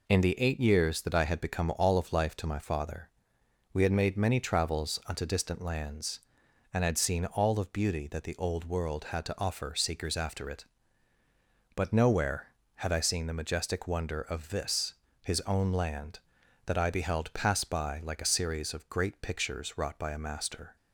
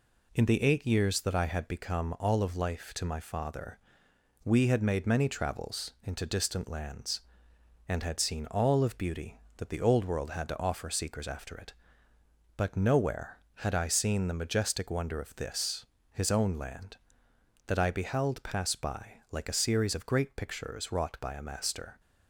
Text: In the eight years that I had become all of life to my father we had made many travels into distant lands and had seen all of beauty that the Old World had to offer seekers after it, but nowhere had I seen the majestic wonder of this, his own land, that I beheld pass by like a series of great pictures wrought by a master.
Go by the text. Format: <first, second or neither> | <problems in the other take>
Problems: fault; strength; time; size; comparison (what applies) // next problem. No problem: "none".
second | pauses between "father" and "we"; noticeable; at 3.0 s; 0.64 s long; noticeable in the second // says "unto" for "into"; at 5.0 s